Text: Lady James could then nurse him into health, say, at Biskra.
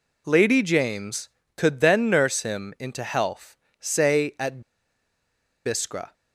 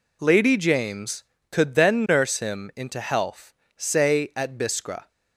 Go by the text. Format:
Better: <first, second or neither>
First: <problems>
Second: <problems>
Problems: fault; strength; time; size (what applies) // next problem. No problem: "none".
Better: second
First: pauses between "at" and "Biskra"; at 4.6 s; 1.0 s long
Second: none